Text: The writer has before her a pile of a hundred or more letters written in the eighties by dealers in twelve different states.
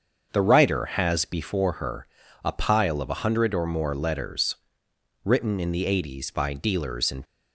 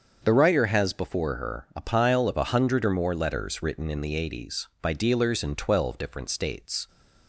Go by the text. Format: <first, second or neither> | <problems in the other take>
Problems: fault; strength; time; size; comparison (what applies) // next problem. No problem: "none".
second | starts louder than the rest; until 1.3 s; 6.5 dB; also in the second // pauses between "her" and "a"; at 2.0 s; 0.40 s long // pauses between "letters" and "written"; noticeable; at 4.5 s; 0.70 s long // stops before "twelve different states"; at 7.2 s